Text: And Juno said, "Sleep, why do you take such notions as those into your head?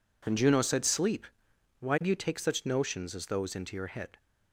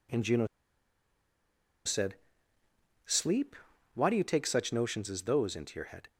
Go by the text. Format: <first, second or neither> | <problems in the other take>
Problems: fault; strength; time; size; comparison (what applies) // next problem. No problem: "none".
first | pauses between "Juno" and "said"; strong; at 0.4 s; 1.3 s long